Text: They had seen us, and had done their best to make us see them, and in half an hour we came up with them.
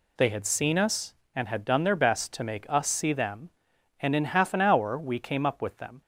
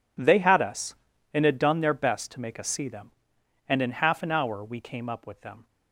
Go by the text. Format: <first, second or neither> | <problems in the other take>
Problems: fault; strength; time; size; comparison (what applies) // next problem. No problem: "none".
first | skips "seen"; at 0.5 s